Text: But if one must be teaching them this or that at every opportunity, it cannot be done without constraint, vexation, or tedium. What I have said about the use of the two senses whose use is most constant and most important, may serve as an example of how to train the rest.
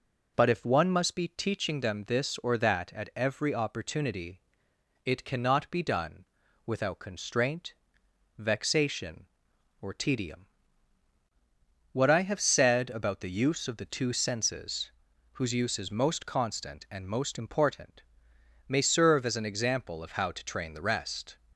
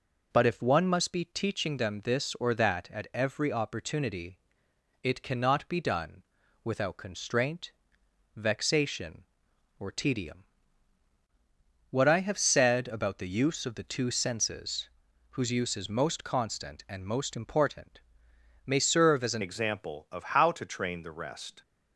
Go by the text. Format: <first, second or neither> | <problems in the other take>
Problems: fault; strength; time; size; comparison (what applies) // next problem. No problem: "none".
first | pauses between "done" and "without"; at 6.2 s; 0.42 s long; also in the first // pauses between "senses" and "whose"; at 14.8 s; 0.44 s long; also in the first // changes voice at "example"; from 19.4 s on; 2.2 s long